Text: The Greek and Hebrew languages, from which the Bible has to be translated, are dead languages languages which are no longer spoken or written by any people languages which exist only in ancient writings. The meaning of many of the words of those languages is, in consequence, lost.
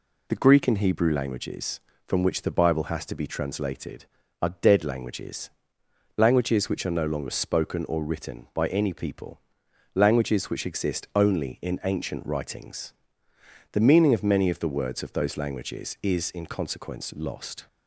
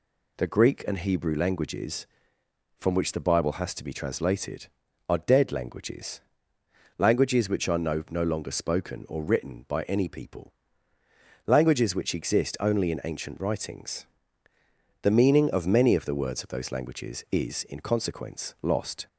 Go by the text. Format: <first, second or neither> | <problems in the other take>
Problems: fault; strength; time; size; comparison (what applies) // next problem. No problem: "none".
first | pauses between "languages" and "languages"; noticeable; at 6.2 s; 0.78 s long; noticeable in the first // says "no" twice; at 8.0 s // pauses between "people" and "languages"; noticeable; at 10.5 s; 0.94 s long; noticeable in the first